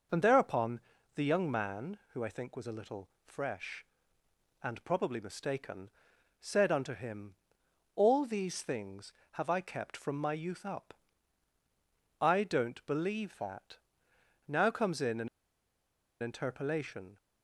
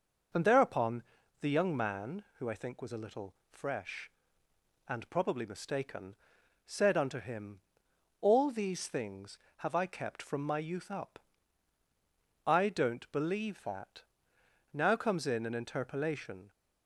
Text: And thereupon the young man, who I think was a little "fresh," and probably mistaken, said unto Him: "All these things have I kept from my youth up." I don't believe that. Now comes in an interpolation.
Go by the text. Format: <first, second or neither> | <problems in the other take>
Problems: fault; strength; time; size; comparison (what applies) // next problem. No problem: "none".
second | pauses between "thereupon" and "the"; slight; at 0.8 s; 0.34 s long; also in the second // pauses between "little" and "fresh"; slight; at 3.0 s; 0.16 s long; slight in the second // pauses between "an" and "interpolation"; noticeable; at 15.2 s; 0.92 s long